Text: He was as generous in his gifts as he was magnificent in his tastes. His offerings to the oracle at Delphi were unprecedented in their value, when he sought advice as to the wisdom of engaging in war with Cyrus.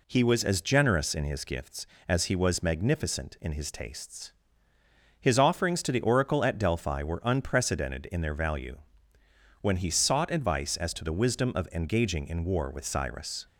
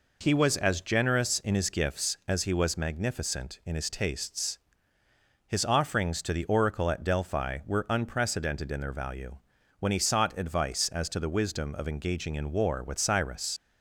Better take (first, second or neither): first